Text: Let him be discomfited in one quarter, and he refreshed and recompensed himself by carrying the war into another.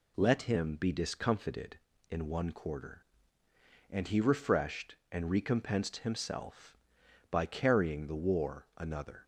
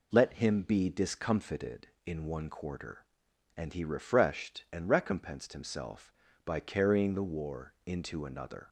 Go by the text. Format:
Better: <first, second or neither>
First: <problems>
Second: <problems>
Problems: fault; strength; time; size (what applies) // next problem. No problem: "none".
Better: second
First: skips "into"; at 8.7 s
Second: none